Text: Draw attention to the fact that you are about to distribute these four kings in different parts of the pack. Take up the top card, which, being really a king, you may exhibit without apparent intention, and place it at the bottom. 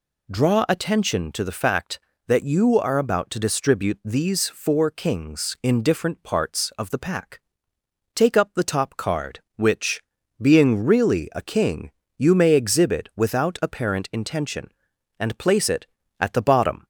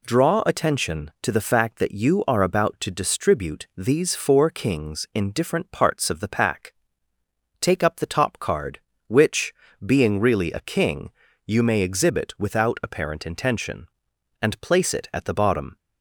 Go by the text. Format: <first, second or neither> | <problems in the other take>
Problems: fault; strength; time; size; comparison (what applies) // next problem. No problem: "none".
neither | none